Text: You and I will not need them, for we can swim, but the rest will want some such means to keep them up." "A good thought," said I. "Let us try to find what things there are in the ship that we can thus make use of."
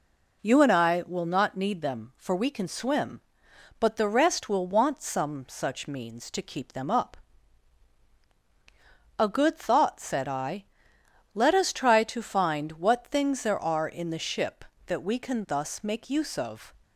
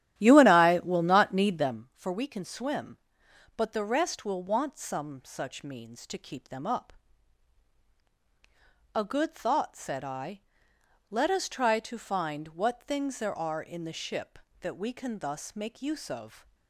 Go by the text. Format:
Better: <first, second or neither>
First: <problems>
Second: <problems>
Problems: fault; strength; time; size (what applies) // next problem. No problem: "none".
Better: first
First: none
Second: starts louder than the rest; strong; until 1.9 s; 12 dB